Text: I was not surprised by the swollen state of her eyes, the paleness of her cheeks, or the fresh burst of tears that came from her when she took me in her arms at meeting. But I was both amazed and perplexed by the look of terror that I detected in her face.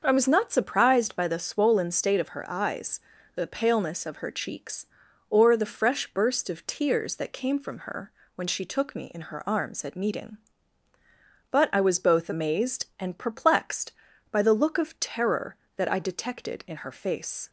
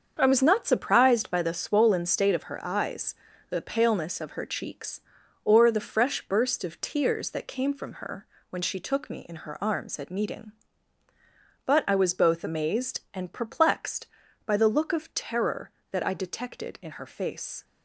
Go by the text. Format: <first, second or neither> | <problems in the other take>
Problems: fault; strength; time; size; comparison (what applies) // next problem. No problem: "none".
first | gets quieter; strong; throughout; 8.5 dB // starts louder than the rest; until 1.2 s; 7 dB; also in the first // pauses between "her" and "when"; slight; at 8.2 s; 0.24 s long; slight in the first